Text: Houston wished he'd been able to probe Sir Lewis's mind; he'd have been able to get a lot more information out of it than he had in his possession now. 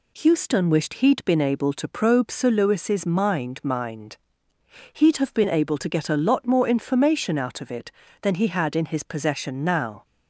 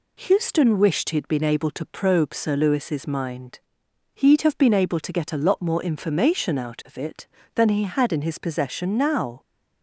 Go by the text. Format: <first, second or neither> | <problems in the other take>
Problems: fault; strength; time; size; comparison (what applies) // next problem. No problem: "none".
second | says "mind" twice; at 3.6 s